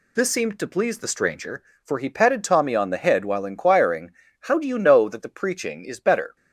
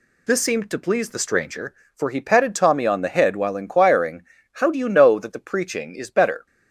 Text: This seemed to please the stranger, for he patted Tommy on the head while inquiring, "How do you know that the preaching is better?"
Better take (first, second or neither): neither